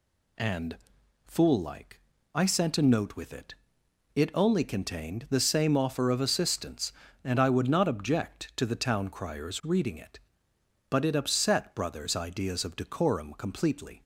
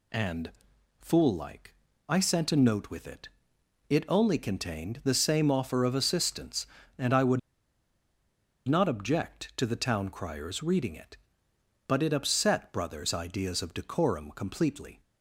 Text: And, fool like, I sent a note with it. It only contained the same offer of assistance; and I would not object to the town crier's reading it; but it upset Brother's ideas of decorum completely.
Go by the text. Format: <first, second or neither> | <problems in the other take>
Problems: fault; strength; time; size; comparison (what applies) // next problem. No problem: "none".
first | pauses between "would" and "not"; strong; at 7.3 s; 1.2 s long